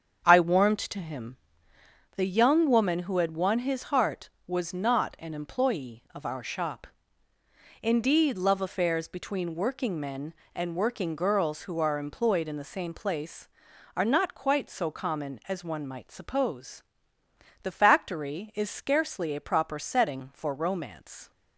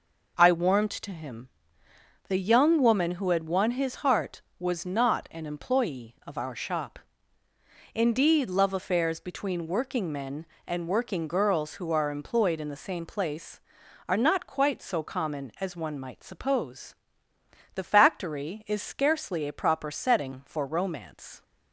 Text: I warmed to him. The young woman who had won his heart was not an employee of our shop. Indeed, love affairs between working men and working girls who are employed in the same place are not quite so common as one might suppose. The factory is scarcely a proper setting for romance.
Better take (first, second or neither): second